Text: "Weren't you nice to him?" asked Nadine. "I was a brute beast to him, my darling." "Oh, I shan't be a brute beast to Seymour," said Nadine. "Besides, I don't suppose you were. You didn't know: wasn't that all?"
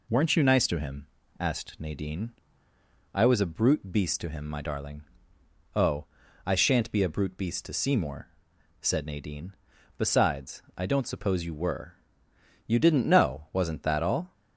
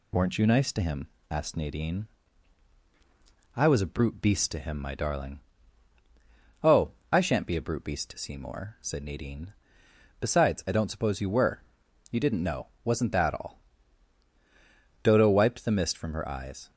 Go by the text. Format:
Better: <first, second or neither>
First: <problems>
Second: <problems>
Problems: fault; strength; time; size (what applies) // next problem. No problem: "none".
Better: first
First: none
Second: goes on to say "Dodo wiped the mist from her eyes"; strong; from 15.0 s on; 1.6 s long